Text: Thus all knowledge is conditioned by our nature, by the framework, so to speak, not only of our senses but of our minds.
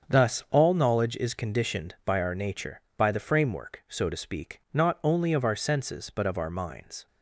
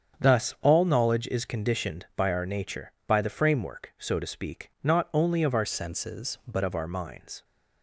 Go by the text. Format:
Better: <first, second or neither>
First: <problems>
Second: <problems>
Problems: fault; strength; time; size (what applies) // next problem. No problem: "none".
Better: first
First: starts louder than the rest; strong; until 1.1 s; 7 dB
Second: starts louder than the rest; strong; until 1.2 s; 8 dB // changes voice from "senses" to "but"; from 5.6 to 6.6 s; 1.0 s long